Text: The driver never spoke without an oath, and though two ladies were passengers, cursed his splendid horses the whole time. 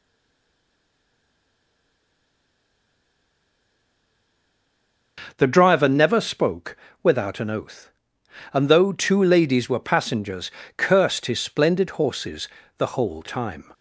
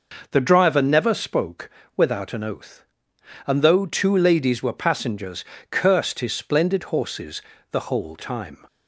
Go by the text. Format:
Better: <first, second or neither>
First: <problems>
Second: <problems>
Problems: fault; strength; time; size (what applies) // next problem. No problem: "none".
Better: second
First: stays silent before the first word; strong; until 5.1 s; 5.1 s long // pauses between "spoke" and "without"; slight; at 6.7 s; 0.26 s long // pauses between "horses" and "the"; slight; at 12.4 s; 0.30 s long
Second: pauses between "spoke" and "without"; slight; at 1.7 s; 0.26 s long // pauses between "horses" and "the"; slight; at 7.4 s; 0.30 s long